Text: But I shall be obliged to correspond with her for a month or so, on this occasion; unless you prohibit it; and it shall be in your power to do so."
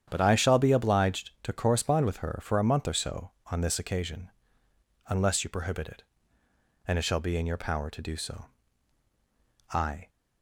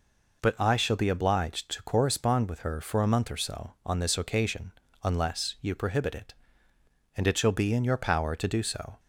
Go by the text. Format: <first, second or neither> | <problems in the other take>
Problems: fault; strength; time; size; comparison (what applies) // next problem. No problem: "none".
second | starts louder than the rest; strong; until 1.1 s; 9 dB // goes on to say "I"; slight; from 9.7 s on; 0.38 s long